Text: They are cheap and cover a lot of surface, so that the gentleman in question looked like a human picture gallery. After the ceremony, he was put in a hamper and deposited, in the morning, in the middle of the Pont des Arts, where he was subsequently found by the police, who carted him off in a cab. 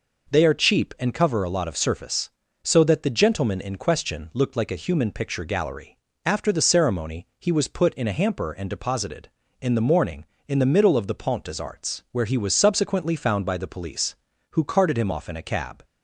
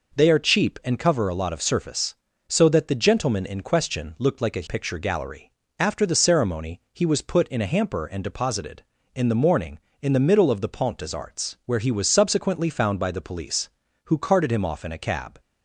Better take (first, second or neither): first